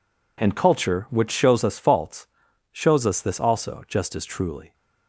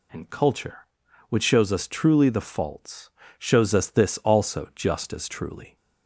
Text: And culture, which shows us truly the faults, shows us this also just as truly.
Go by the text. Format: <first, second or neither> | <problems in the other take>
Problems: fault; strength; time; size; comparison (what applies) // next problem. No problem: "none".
second | skips "truly the"; at 1.7 s